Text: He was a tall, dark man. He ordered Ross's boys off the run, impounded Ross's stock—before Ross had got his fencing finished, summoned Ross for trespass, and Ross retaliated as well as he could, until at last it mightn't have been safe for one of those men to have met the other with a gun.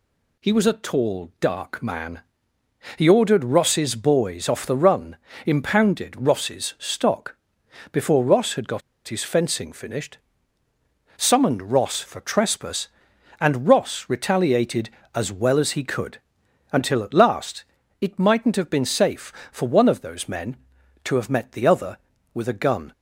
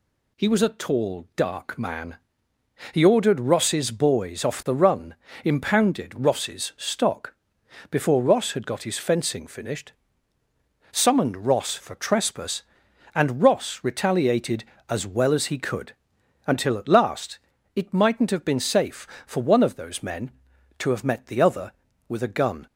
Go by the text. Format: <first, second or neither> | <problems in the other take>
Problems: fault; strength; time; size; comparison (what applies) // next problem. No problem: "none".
second | pauses between "got" and "his"; slight; at 8.8 s; 0.26 s long // pauses between "last" and "it"; slight; at 17.6 s; 0.36 s long; slight in the second